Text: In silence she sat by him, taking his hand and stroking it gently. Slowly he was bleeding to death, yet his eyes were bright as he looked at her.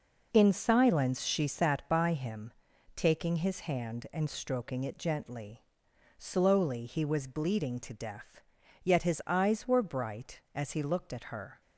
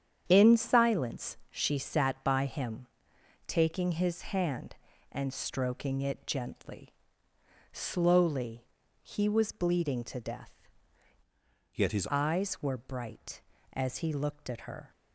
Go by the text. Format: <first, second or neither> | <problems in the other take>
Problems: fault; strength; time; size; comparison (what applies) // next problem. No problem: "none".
first | starts louder than the rest; strong; until 1.2 s; 8.5 dB // pauses between "Slowly" and "he"; at 8.6 s; 0.38 s long // changes voice from "yet" to "his"; from 11.7 to 12.0 s; 0.3 s long